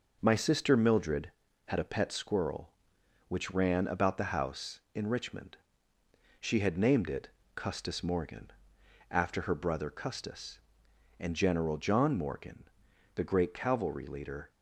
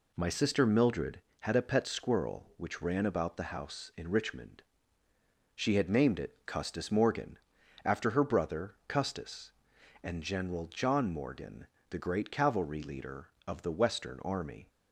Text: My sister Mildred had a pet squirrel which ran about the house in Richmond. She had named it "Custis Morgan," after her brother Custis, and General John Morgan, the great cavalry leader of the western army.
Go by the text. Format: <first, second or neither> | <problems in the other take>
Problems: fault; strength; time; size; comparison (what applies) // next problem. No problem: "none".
second | pauses between "it" and "Custis"; slight; at 7.2 s; 0.26 s long // stops before "of the western army"; at 14.5 s